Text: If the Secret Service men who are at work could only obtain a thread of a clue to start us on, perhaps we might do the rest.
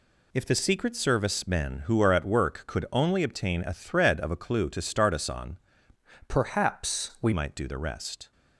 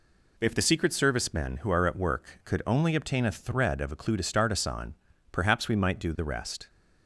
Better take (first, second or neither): second